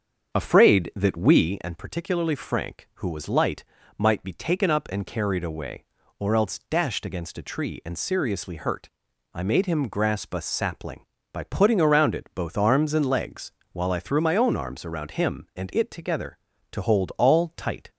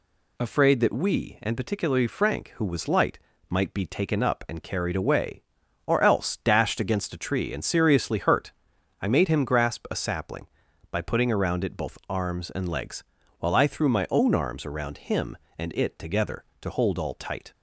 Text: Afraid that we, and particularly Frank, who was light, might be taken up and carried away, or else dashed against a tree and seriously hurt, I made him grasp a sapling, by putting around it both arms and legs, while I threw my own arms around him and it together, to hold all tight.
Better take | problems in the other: second | starts louder than the rest; until 1.6 s; 7 dB

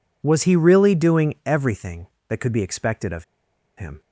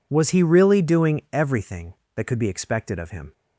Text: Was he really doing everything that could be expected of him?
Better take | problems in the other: second | pauses between "of" and "him"; noticeable; at 3.2 s; 0.54 s long

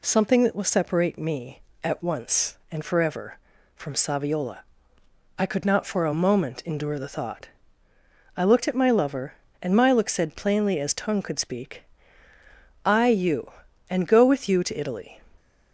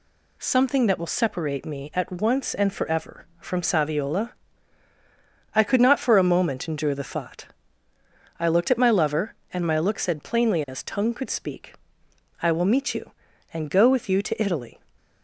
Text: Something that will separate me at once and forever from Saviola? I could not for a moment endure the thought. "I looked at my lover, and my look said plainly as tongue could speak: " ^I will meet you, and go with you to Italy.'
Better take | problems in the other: second | skips "will meet"; at 13.0 s

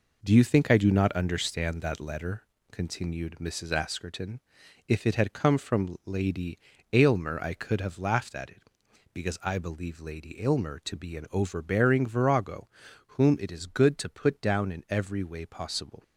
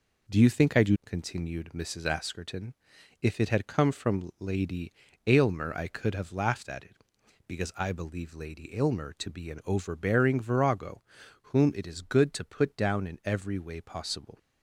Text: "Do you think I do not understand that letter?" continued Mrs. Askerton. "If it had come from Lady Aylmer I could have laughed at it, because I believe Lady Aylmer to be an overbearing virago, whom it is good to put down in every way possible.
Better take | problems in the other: first | skips "not understand that letter"; at 1.0 s // pauses between "Lady" and "Aylmer"; slight; at 4.9 s; 0.32 s long; slight in the first

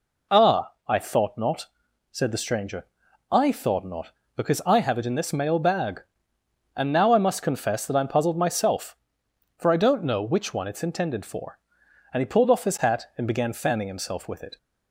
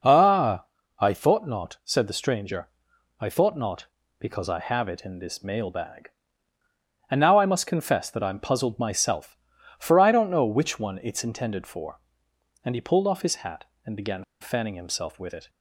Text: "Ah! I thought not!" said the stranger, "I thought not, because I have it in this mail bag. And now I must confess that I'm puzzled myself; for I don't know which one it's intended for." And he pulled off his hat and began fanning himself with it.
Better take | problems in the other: first | pauses between "began" and "fanning"; slight; at 14.2 s; 0.17 s long

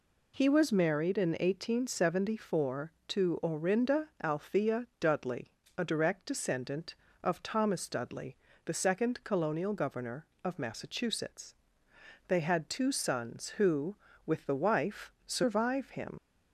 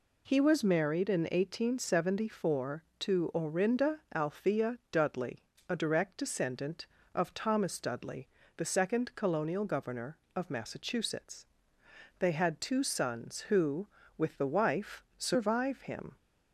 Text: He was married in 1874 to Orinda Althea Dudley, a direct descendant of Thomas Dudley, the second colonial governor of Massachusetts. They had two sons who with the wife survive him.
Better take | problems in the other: second | leaves "him" unfinished; at 16.1 s; 65 ms

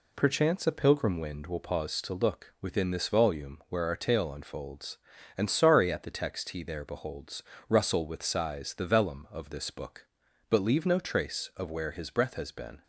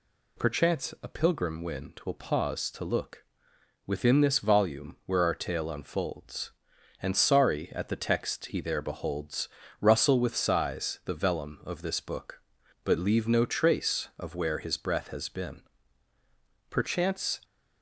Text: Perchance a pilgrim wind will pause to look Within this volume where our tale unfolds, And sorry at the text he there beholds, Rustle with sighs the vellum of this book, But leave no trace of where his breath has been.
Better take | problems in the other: first | pauses between "look" and "Within"; noticeable; at 3.2 s; 0.64 s long // goes on to say "Perchance"; noticeable; from 16.6 s on; 0.70 s long

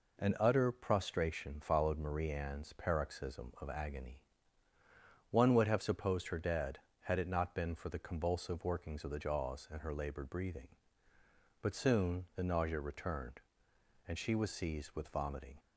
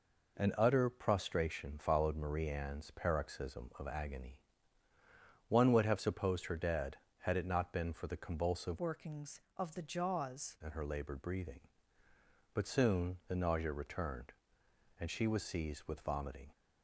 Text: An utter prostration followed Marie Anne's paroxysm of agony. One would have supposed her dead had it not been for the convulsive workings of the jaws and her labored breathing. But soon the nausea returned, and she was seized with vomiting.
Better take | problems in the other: first | changes voice from "workings" to "jaws"; from 8.7 to 10.5 s; 1.8 s long

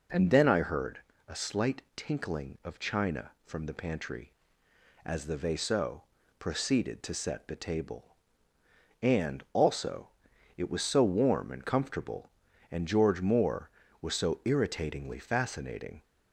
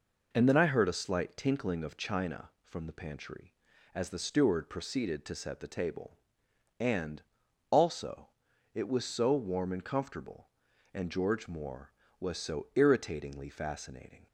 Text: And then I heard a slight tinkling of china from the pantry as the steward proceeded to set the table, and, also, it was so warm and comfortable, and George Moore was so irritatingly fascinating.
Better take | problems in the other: second | pauses between "heard" and "a"; slight; at 0.9 s; 0.30 s long // says "vaisseau" for "steward"; at 5.3 s

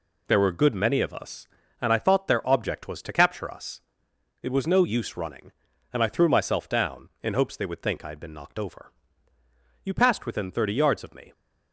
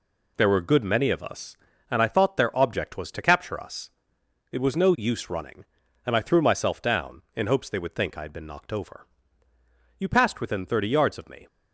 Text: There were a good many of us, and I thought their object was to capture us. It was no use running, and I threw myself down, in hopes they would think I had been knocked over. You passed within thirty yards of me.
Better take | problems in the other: neither | none

